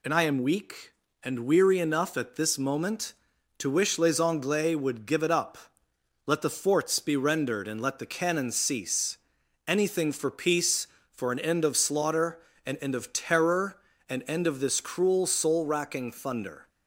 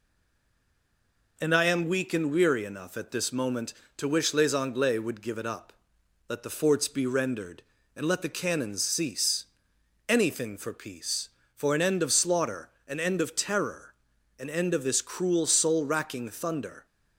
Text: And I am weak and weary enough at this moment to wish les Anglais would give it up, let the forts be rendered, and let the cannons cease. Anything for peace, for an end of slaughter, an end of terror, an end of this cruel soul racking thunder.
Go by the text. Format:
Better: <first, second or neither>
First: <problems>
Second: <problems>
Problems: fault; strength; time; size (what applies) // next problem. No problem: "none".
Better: first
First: none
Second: stays silent before the first word; noticeable; until 1.3 s; 1.3 s long